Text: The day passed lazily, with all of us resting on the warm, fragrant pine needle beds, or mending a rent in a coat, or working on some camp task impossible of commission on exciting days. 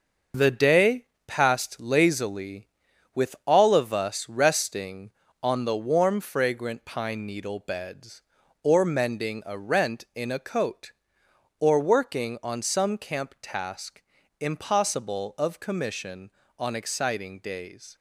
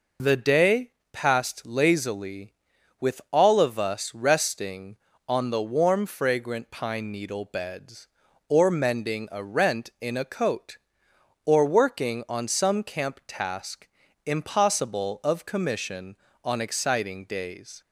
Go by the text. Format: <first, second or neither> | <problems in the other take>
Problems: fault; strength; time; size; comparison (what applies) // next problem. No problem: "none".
second | gets quieter; throughout; 6.5 dB // pauses between "day" and "passed"; slight; at 1.0 s; 0.22 s long; slight in the second // pauses between "task" and "impossible"; at 14.0 s; 0.40 s long; also in the second